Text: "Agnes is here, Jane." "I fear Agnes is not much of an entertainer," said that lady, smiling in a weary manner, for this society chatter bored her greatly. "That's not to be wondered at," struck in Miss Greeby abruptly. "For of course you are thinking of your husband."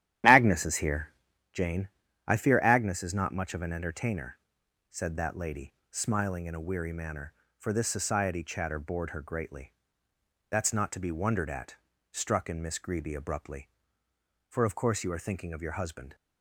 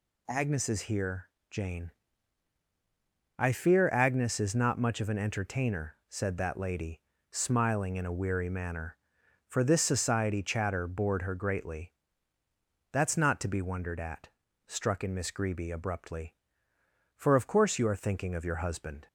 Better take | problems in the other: second | starts louder than the rest; strong; until 1.6 s; 11.5 dB

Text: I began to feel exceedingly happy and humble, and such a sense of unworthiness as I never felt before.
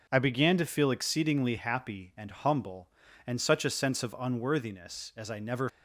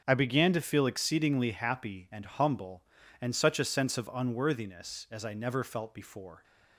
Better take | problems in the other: second | starts louder than the rest; until 1.1 s; 6.5 dB; noticeable in the second // stops before "felt before"; at 5.6 s

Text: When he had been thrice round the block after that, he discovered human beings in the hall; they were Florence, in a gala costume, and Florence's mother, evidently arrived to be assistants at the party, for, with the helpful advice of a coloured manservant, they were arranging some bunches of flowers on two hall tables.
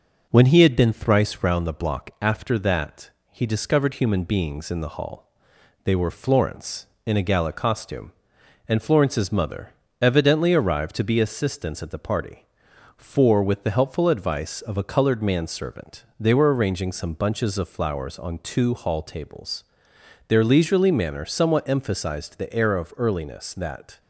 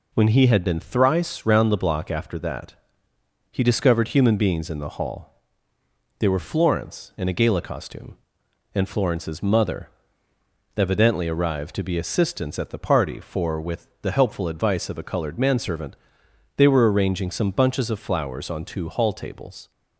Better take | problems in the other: second | goes on to say "Their leisurely manner somewhat emphasized the air of earliness that"; strong; from 20.2 s on; 3.7 s long

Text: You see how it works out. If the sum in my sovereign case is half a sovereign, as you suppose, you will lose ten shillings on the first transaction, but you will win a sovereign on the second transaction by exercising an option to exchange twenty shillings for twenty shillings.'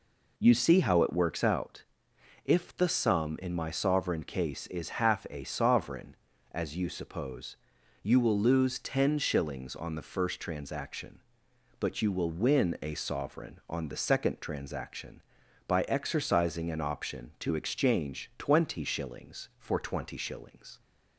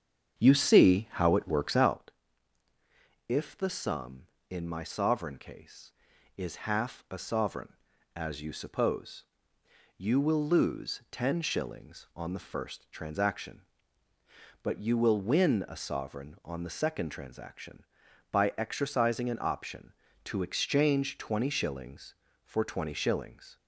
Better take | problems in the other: first | starts louder than the rest; strong; until 2.0 s; 7.5 dB

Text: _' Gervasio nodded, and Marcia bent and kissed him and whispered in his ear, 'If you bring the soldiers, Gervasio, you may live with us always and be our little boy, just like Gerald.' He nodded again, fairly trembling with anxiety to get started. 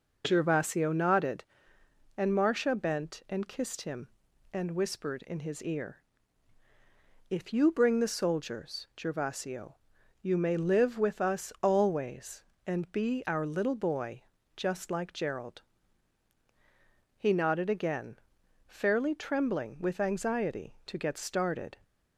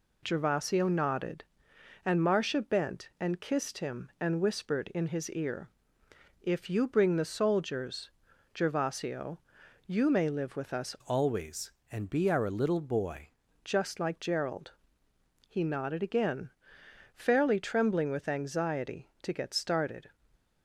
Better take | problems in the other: first | changes voice from "always" to "boy"; from 11.0 to 13.2 s; 2.2 s long // stays silent after the last word; slight; from 20.1 s on; 0.5 s long

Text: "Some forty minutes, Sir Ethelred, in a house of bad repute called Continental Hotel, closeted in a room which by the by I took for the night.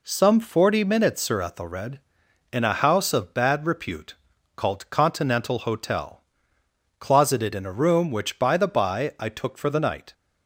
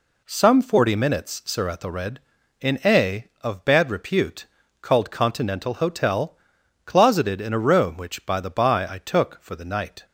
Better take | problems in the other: first | skips "house"; at 3.3 s // pauses between "repute" and "called"; slight; at 4.4 s; 0.36 s long; also in the first

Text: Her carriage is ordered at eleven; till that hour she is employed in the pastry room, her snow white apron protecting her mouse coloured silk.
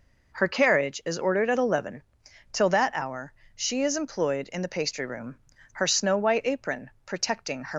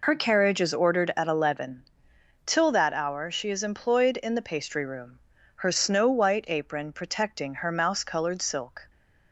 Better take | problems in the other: second | pauses between "hour" and "she"; slight; at 3.3 s; 0.20 s long // stops before "mouse coloured silk"; at 7.7 s

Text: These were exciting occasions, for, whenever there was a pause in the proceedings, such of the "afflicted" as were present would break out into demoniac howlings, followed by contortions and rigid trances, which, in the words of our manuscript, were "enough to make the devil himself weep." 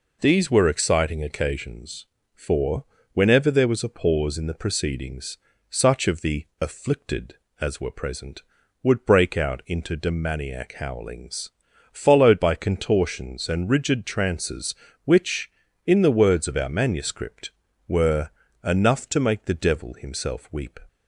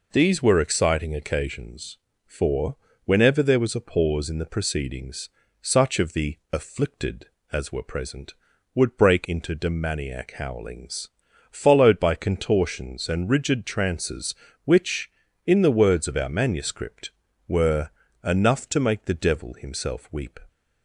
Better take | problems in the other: first | pauses between "the" and "afflicted"; slight; at 6.3 s; 0.16 s long; slight in the first // skips "out"; at 9.2 s // pauses between "were" and "enough"; slight; at 17.9 s; 0.32 s long; slight in the first

